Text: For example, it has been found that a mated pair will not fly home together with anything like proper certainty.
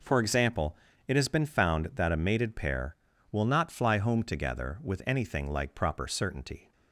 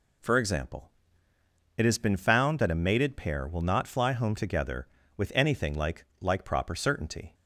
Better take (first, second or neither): first